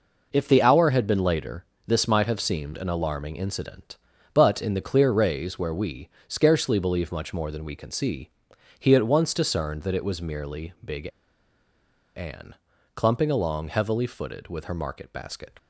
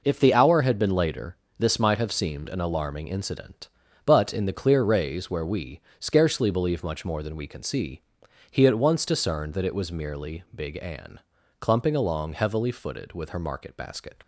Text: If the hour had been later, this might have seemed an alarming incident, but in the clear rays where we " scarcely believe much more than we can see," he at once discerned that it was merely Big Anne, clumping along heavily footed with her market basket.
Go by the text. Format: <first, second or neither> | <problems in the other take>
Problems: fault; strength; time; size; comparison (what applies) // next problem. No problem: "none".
second | pauses between "Big" and "Anne"; at 11.0 s; 1.0 s long